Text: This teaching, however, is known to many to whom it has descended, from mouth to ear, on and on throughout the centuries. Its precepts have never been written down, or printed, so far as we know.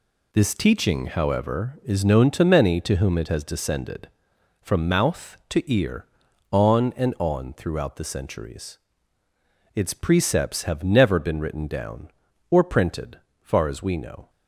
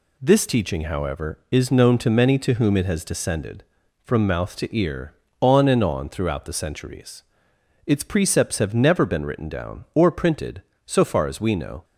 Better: second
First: skips "so"; at 13.2 s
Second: none

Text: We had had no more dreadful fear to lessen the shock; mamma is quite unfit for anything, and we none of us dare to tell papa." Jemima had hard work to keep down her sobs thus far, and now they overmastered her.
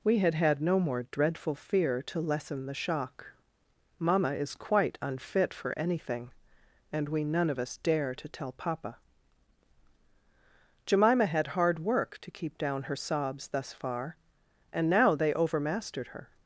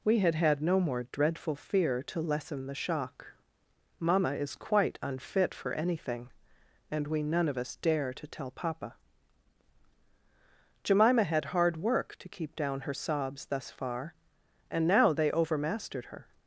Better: neither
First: none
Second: none

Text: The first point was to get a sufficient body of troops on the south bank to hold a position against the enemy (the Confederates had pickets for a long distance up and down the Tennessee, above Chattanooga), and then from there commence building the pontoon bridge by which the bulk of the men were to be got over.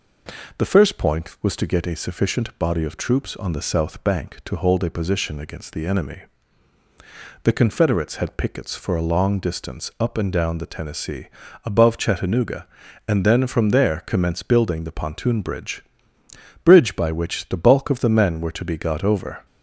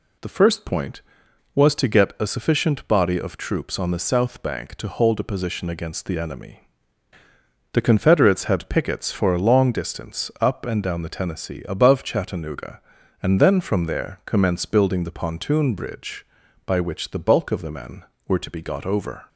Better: second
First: says "bridge" twice; at 16.6 s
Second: none

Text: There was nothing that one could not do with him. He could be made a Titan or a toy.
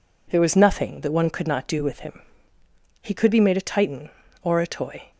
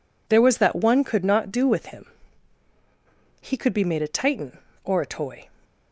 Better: first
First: none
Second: skips "nothing"; at 0.5 s

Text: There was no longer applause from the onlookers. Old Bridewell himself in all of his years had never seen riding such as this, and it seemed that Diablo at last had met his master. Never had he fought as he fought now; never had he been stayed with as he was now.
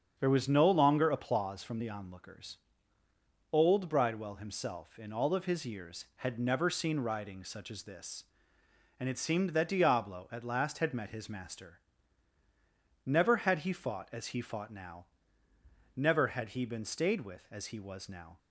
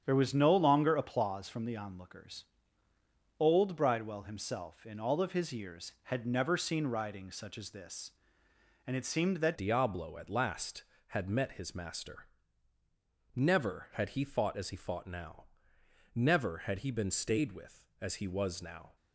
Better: first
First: starts louder than the rest; until 1.2 s; 7 dB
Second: starts louder than the rest; strong; until 1.0 s; 8 dB // changes voice at "Diablo"; from 9.5 s on; 9.4 s long

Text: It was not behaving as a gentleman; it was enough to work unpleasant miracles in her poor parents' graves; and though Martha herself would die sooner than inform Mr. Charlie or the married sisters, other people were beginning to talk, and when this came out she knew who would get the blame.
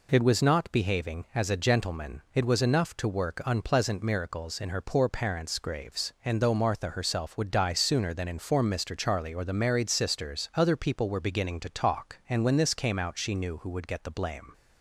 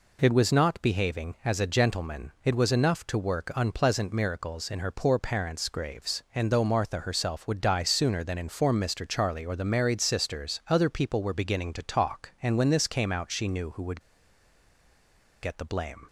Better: first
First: none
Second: pauses between "would" and "get"; strong; at 14.0 s; 1.4 s long

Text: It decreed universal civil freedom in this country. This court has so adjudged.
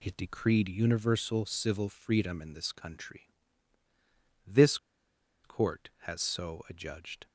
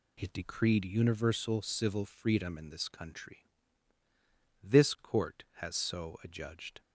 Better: second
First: pauses between "This" and "court"; noticeable; at 4.7 s; 0.67 s long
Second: none

